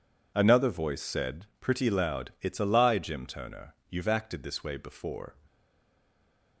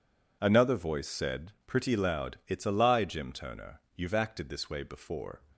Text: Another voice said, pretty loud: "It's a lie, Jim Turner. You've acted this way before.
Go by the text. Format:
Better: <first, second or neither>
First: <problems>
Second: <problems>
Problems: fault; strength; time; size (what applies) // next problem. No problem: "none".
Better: second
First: stays silent after the last word; noticeable; from 5.4 s on; 1.2 s long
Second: none